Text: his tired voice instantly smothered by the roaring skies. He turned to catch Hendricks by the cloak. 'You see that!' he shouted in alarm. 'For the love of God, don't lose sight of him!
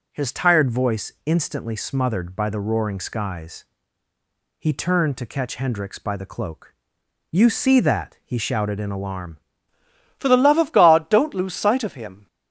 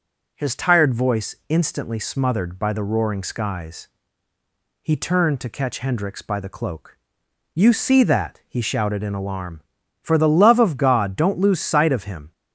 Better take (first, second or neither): second